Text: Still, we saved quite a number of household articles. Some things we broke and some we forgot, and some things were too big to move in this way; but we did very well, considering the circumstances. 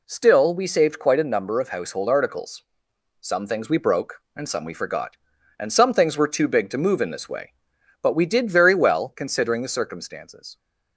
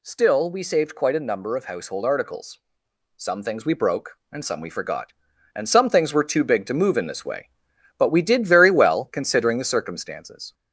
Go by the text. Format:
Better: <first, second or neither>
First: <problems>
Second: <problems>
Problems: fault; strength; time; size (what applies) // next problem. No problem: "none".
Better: first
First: none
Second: gets louder; slight; throughout; 2.5 dB